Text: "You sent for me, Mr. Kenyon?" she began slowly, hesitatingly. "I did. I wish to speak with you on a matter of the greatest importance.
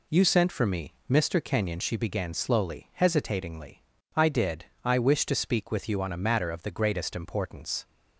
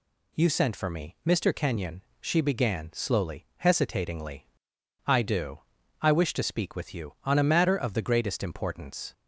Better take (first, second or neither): first